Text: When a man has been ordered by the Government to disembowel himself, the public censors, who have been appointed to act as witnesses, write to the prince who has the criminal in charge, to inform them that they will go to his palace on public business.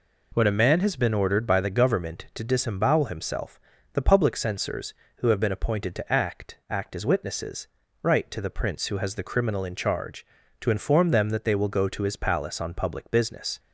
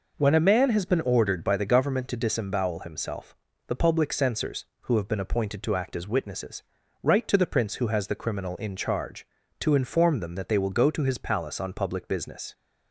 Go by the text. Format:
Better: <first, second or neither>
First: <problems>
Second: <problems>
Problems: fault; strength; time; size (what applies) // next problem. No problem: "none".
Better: second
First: says "act" twice; at 6.7 s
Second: none